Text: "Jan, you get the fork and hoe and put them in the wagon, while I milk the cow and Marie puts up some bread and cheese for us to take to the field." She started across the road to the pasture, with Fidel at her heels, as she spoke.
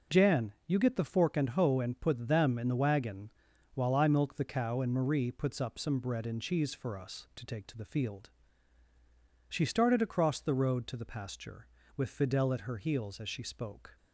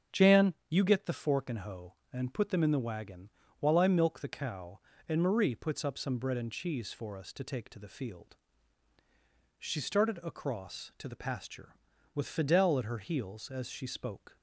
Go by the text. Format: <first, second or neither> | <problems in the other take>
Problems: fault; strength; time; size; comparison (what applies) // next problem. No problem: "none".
first | starts louder than the rest; until 1.2 s; 7 dB // skips "the road"; at 10.9 s